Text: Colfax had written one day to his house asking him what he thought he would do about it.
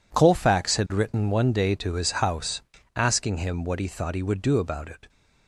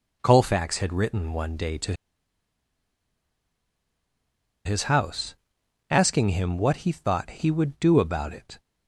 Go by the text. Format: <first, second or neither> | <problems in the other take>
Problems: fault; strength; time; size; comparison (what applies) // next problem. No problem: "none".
first | pauses between "to" and "his"; strong; at 1.9 s; 2.7 s long // pauses between "house" and "asking"; noticeable; at 5.3 s; 0.56 s long; slight in the first